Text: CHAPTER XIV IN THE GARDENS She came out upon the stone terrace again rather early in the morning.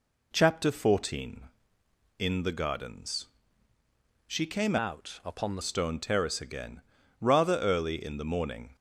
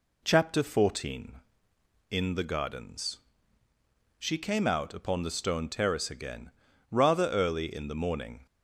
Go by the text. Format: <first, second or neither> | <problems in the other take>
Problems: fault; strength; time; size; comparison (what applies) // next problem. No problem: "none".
second | pauses between "GARDENS" and "She"; at 3.2 s; 1.0 s long; also in the second // changes voice from "out" to "the"; from 4.7 to 5.6 s; 0.9 s long // pauses between "again" and "rather"; at 6.8 s; 0.38 s long; also in the second